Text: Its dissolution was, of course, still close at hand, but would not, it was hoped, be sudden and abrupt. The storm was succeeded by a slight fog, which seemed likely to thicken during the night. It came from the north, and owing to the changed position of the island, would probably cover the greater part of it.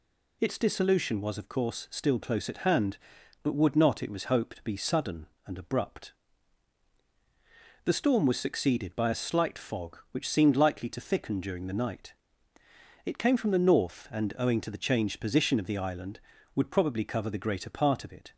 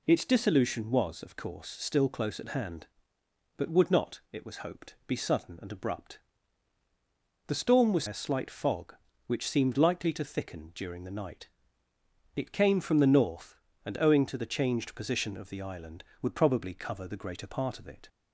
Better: first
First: none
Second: skips "succeeded by"; at 8.0 s

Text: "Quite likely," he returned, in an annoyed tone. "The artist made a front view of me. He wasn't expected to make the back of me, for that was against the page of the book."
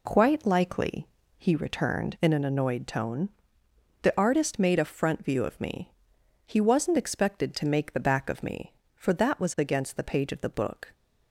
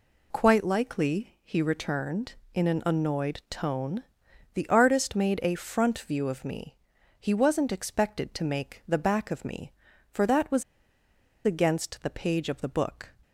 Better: first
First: none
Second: pauses between "was" and "against"; noticeable; at 10.6 s; 0.81 s long

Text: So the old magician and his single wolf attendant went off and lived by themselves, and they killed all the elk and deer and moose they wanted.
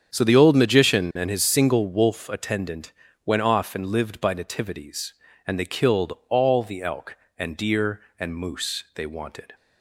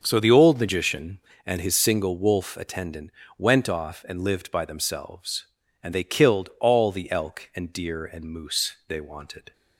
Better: second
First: starts louder than the rest; strong; until 1.1 s; 7.5 dB // pauses between "attendant" and "went"; slight; at 2.9 s; 0.32 s long // says "nativities" for "themselves"; at 4.3 s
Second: starts louder than the rest; until 1.0 s; 6.5 dB // pauses between "attendant" and "went"; slight; at 3.1 s; 0.26 s long

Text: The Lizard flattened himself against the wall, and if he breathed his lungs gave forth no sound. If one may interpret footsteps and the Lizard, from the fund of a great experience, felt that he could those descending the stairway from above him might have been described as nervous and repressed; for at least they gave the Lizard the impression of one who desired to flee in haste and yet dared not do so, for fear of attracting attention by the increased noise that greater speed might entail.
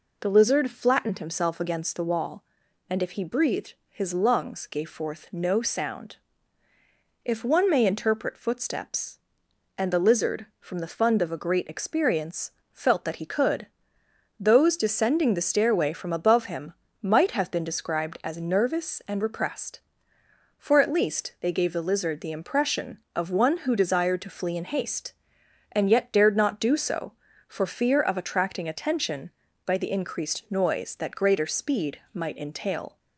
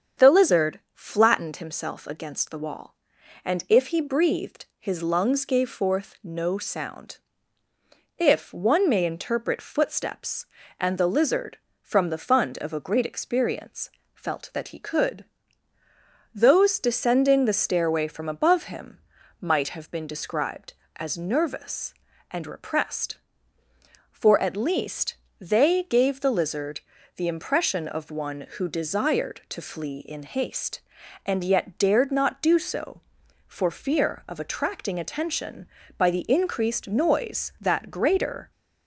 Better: first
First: pauses between "could" and "those"; noticeable; at 13.6 s; 0.74 s long // pauses between "him" and "might"; slight; at 16.7 s; 0.28 s long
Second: starts louder than the rest; strong; until 1.3 s; 7.5 dB // pauses between "could" and "those"; at 15.2 s; 1.1 s long // pauses between "him" and "might"; at 18.9 s; 0.42 s long // pauses between "least" and "they"; slight; at 25.1 s; 0.26 s long // pauses between "Lizard" and "the"; slight; at 26.8 s; 0.36 s long // stops before "speed might entail"; at 38.5 s

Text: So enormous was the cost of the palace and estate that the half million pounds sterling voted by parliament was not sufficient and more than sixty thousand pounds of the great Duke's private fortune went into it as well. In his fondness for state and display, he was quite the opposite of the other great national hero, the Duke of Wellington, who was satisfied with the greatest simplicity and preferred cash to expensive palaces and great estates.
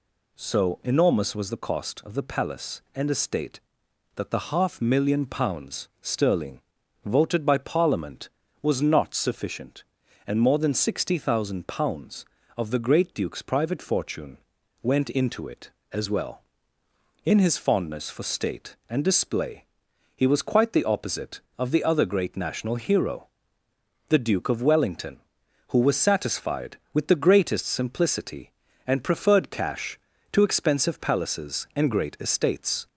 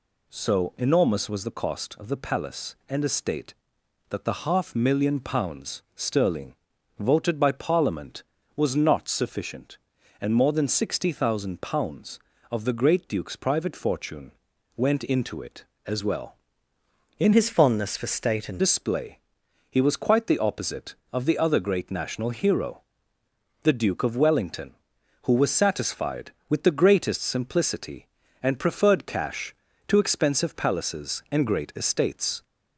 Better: first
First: pauses between "sterling" and "voted"; at 6.5 s; 0.44 s long // pauses between "fortune" and "went"; at 14.3 s; 0.44 s long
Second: pauses between "sterling" and "voted"; at 6.5 s; 0.44 s long // pauses between "fortune" and "went"; at 14.3 s; 0.44 s long // changes voice from "his" to "and"; from 17.3 to 18.6 s; 1.3 s long

